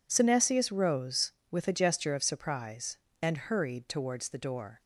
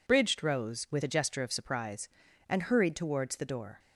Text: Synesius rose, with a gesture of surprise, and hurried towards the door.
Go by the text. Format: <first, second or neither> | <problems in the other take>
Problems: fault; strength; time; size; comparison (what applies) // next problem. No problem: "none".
first | says "Bridged" for "Synesius"; at 0.0 s